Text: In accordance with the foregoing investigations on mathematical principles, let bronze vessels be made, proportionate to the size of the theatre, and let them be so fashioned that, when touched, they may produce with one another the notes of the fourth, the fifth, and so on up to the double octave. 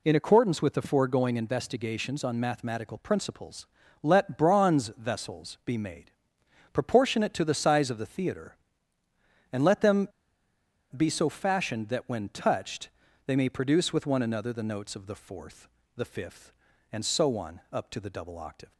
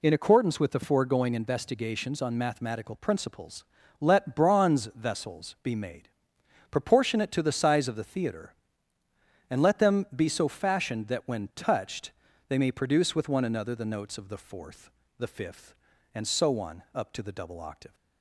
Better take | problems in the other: second | pauses between "them" and "be"; noticeable; at 10.0 s; 0.86 s long

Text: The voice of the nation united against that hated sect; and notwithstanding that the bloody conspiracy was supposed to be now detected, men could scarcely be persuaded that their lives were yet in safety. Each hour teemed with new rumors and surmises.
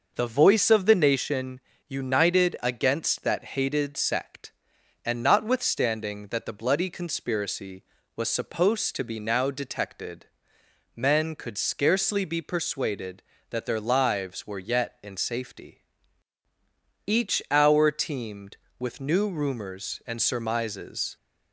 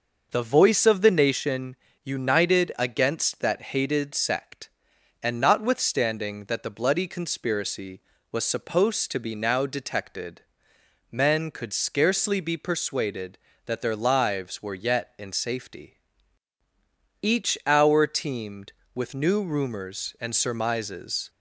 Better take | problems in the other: neither | pauses between "nation" and "united"; slight; the same in both

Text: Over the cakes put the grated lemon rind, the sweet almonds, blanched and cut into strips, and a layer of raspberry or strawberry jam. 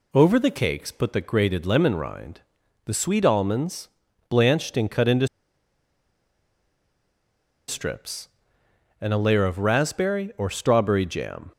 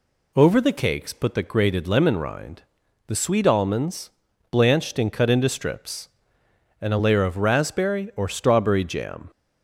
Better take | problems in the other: second | pauses between "into" and "strips"; strong; at 5.2 s; 2.4 s long

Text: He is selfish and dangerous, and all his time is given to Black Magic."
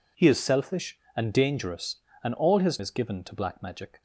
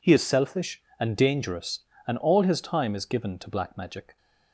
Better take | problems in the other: second | skips "time"; at 2.7 s

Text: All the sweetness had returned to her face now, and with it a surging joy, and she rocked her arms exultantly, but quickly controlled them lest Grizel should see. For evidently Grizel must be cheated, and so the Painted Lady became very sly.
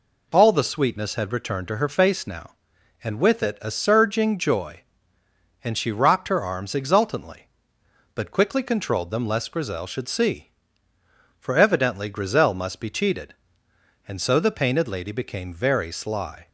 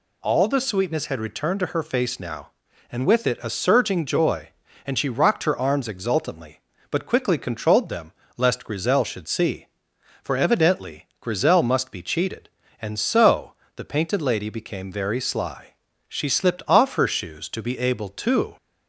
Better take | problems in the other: first | pauses between "them" and "lest"; slight; at 8.1 s; 0.24 s long // pauses between "so" and "the"; slight; at 13.5 s; 0.22 s long // goes on to say "She slipped off her shoes to be able to"; strong; from 16.0 s on; 2.5 s long

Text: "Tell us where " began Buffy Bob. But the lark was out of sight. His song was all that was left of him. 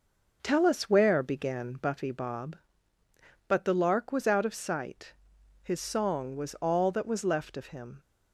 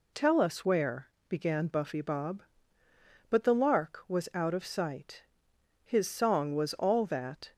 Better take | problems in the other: first | stops before "was left of him"; at 7.5 s

